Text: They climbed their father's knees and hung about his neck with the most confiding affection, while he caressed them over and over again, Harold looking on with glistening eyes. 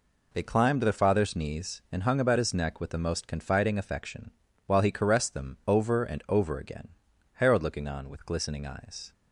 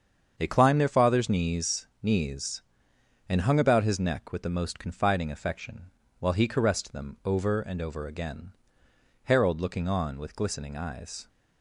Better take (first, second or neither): first